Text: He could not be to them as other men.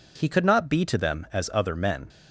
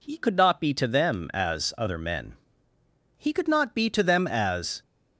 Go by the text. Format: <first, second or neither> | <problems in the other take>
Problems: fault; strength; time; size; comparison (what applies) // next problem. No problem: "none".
first | goes on to say "He could not be to them as"; from 3.1 s on; 1.6 s long